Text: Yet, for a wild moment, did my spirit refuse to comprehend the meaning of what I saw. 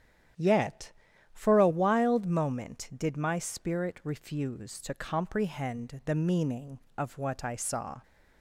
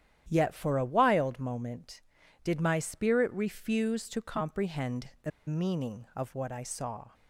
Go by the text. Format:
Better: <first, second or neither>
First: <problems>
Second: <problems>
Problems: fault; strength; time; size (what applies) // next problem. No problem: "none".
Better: first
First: starts louder than the rest; strong; until 1.7 s; 9.5 dB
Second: starts louder than the rest; strong; until 1.2 s; 10.5 dB // pauses between "the" and "meaning"; slight; at 5.3 s; 0.17 s long